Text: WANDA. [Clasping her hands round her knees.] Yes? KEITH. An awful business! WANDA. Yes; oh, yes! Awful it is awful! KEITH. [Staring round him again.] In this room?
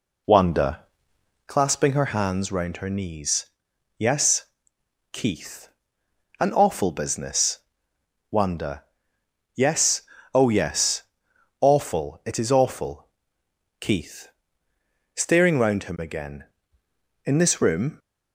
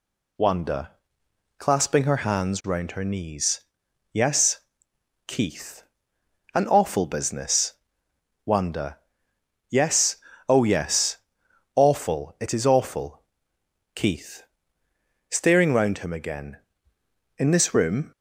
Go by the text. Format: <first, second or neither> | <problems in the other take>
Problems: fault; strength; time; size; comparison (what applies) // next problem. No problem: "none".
second | starts louder than the rest; slight; until 1.6 s; 3 dB